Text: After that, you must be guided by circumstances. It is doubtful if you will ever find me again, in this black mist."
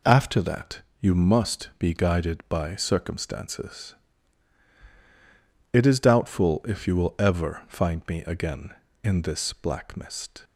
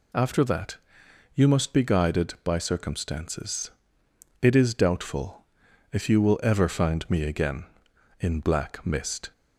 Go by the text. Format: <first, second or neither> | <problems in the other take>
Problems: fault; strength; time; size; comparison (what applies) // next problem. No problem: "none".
first | pauses between "doubtful" and "if"; noticeable; at 5.4 s; 0.48 s long // skips "this"; at 8.3 s